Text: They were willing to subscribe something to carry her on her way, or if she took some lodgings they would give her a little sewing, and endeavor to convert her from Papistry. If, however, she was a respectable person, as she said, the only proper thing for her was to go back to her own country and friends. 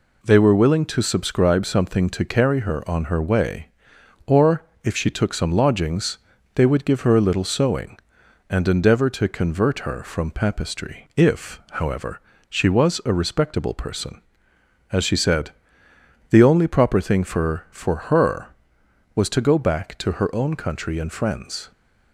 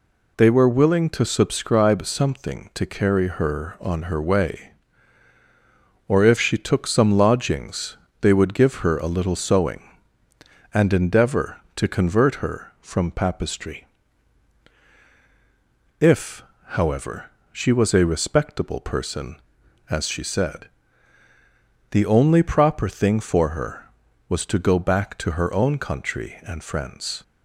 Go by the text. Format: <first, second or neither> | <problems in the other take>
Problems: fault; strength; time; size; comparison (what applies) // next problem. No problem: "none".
second | pauses between "or" and "if"; slight; at 4.6 s; 0.20 s long // pauses between "lodgings" and "they"; slight; at 6.1 s; 0.36 s long; slight in the second // says "for" twice; at 17.7 s